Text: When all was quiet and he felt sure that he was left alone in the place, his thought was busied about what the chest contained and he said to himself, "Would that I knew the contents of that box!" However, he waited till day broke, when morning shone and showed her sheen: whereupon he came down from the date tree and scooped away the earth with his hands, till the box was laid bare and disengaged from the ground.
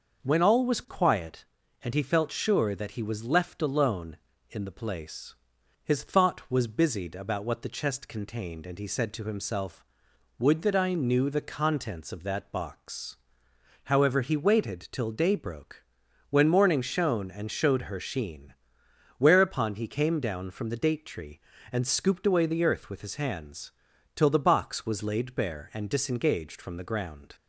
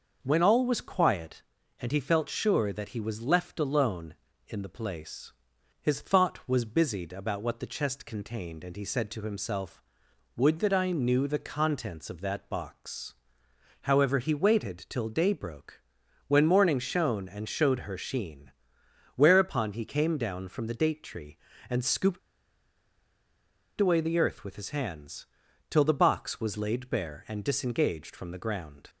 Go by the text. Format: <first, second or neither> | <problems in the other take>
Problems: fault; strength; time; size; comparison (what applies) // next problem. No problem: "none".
first | starts louder than the rest; until 1.2 s; 6 dB; also in the first // pauses between "scooped" and "away"; strong; at 22.1 s; 1.5 s long